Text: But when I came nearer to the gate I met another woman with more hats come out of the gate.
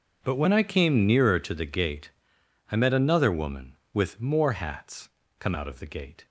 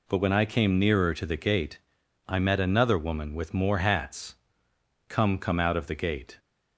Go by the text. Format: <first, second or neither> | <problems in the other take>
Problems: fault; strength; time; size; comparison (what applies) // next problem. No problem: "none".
first | pauses between "gate" and "I"; noticeable; at 1.7 s; 0.50 s long; noticeable in the first // pauses between "hats" and "come"; noticeable; at 4.3 s; 0.72 s long; slight in the first // says "come" twice; at 5.3 s